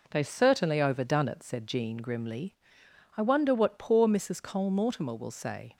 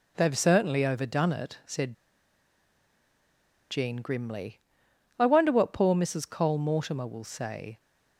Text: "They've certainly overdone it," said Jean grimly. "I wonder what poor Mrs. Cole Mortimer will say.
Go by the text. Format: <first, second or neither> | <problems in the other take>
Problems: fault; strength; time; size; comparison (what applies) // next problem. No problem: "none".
first | pauses between "said" and "Jean"; strong; at 1.9 s; 1.7 s long